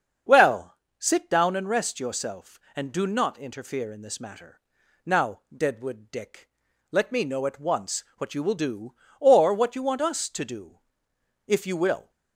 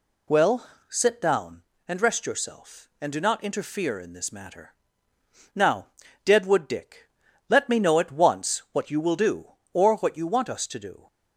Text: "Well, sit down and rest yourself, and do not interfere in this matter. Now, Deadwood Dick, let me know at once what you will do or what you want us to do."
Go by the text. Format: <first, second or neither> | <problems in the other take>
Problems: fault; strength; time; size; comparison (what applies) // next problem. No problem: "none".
second | starts louder than the rest; until 1.5 s; 7 dB // goes on to say "If you will"; noticeable; from 11.4 s on; 0.64 s long